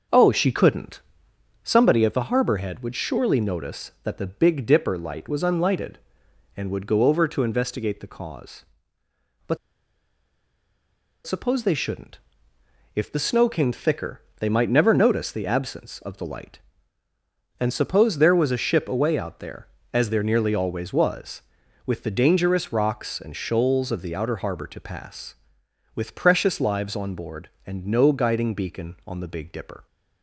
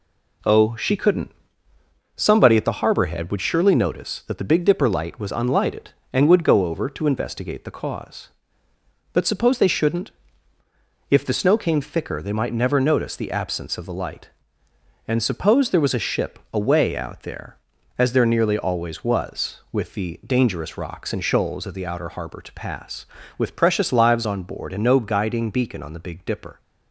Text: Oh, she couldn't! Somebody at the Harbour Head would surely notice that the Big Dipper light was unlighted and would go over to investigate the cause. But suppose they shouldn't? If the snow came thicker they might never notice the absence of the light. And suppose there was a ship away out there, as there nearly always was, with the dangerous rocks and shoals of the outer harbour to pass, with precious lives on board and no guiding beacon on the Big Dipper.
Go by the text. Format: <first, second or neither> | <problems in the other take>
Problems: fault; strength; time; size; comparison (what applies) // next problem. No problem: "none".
second | pauses between "But" and "suppose"; strong; at 9.5 s; 1.7 s long // pauses between "thicker" and "they"; slight; at 14.2 s; 0.18 s long